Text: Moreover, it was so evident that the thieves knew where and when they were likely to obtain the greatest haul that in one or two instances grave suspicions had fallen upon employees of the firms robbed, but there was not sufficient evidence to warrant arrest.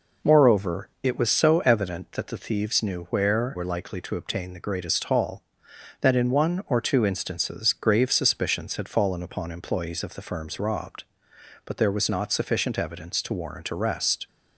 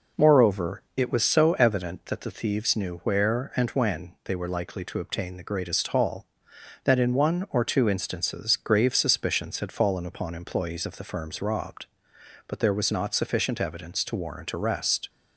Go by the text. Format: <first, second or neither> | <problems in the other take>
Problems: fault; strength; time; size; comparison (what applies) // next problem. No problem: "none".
second | skips "and when they"; at 3.5 s